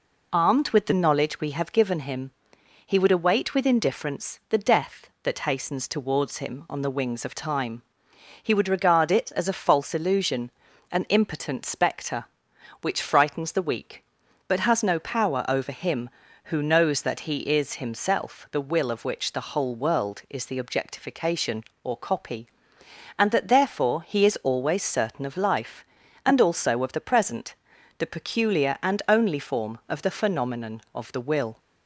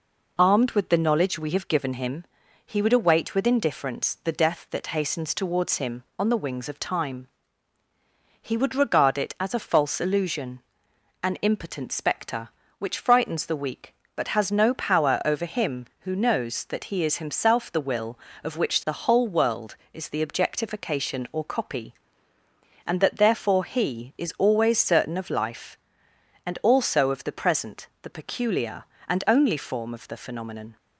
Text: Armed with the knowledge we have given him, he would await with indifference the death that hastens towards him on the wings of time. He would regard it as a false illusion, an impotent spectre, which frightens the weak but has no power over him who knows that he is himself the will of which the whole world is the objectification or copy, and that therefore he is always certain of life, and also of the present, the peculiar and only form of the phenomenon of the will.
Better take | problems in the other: first | stops before "of the will"; at 30.7 s

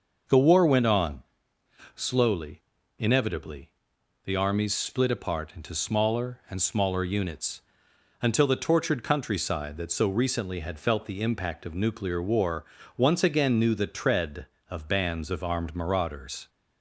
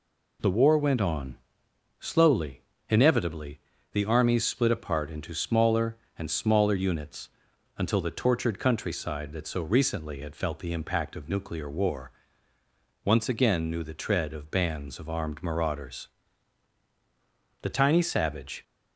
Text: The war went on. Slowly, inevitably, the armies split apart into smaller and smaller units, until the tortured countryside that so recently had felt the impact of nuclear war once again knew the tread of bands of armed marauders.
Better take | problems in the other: first | pauses between "war" and "once"; noticeable; at 12.1 s; 0.92 s long; slight in the first // goes on to say "The tiny savage"; noticeable; from 17.6 s on; 1.0 s long

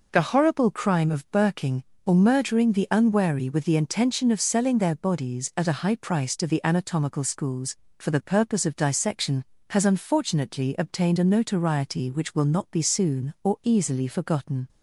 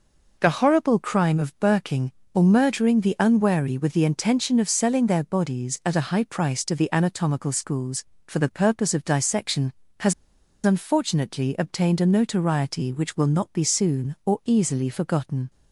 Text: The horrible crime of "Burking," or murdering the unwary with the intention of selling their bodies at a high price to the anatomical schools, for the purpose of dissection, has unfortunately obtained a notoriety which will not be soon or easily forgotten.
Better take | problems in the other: first | pauses between "has" and "unfortunately"; noticeable; at 10.1 s; 0.50 s long

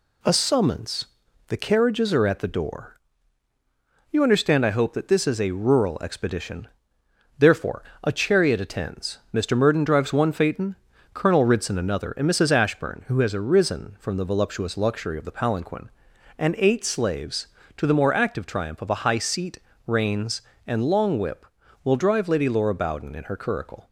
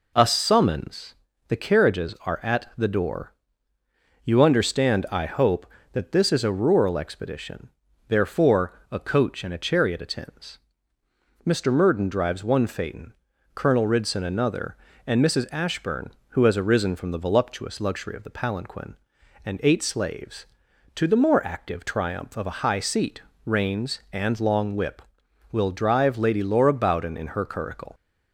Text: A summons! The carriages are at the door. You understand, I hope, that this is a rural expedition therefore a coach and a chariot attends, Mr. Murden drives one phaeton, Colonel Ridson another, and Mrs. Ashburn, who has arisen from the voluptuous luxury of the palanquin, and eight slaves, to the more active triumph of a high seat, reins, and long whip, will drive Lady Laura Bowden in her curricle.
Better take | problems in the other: second | pauses between "expedition" and "therefore"; noticeable; at 6.6 s; 0.72 s long; also in the second // skips "a coach and"; at 7.9 s

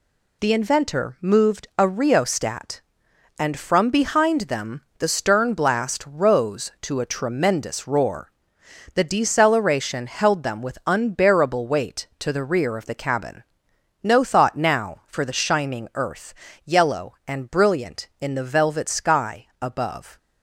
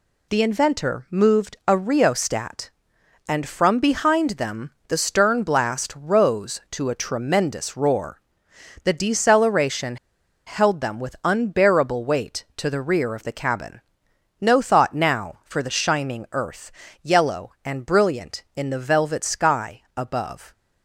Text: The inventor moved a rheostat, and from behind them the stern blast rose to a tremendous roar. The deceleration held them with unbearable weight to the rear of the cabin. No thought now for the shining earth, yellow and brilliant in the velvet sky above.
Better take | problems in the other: first | pauses between "them" and "the"; slight; at 4.7 s; 0.16 s long; slight in the first // pauses between "deceleration" and "held"; noticeable; at 9.9 s; 0.50 s long // pauses between "sky" and "above"; slight; at 19.8 s; 0.16 s long; slight in the first

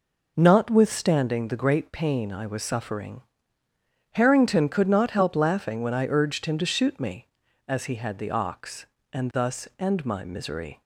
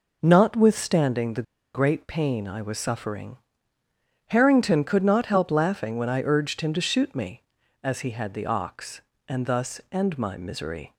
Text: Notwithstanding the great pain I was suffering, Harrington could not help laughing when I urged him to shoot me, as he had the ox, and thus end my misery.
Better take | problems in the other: first | pauses between "the" and "great"; slight; at 1.4 s; 0.30 s long

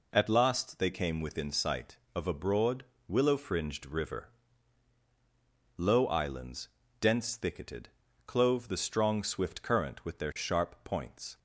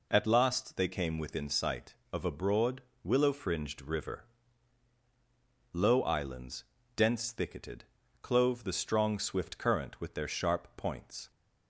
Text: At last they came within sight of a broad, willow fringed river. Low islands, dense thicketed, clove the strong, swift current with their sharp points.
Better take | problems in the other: neither | none

